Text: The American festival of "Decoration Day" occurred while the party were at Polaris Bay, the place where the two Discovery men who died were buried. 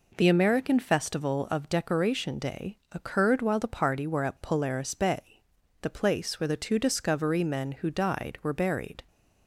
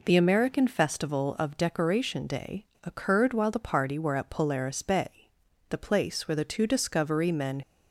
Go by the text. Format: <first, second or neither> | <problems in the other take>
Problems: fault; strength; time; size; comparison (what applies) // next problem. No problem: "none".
first | pauses between "Day" and "occurred"; slight; at 2.6 s; 0.17 s long // stops before "who died were buried"; at 7.6 s